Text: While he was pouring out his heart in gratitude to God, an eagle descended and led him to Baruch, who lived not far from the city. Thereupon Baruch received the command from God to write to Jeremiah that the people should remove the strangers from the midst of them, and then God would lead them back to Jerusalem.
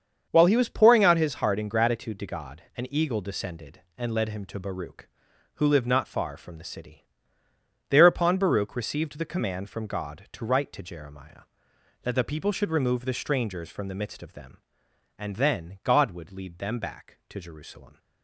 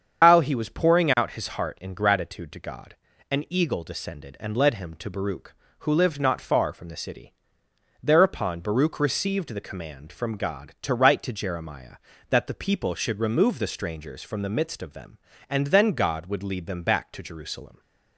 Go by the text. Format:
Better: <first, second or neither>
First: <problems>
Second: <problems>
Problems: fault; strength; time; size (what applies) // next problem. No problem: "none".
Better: first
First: starts louder than the rest; strong; until 1.3 s; 7 dB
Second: loses the start of "While"; at 0.2 s; 175 ms // starts louder than the rest; strong; until 1.2 s; 8 dB